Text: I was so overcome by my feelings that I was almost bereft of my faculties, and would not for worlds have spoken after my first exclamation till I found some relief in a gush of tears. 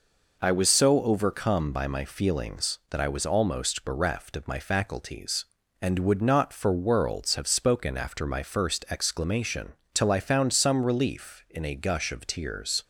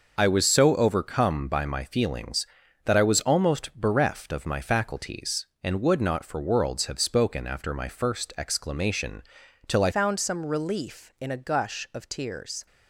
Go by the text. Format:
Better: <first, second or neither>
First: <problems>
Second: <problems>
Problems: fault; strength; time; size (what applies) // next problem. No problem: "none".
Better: first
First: pauses between "exclamation" and "till"; slight; at 9.7 s; 0.18 s long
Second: pauses between "exclamation" and "till"; noticeable; at 9.2 s; 0.46 s long // changes voice at "found"; from 9.9 s on; 2.7 s long